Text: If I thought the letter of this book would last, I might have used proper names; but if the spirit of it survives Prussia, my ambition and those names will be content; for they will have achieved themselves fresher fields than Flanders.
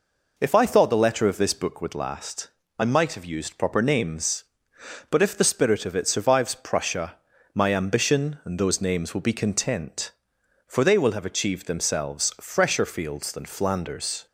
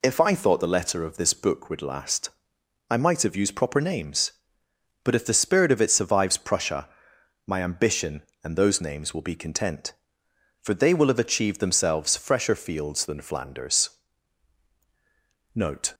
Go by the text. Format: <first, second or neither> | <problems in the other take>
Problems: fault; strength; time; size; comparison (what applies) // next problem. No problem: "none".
first | goes on to say "Note"; slight; from 15.5 s on; 0.38 s long